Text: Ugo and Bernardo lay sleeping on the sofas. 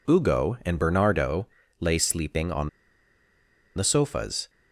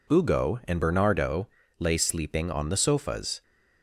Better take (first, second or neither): second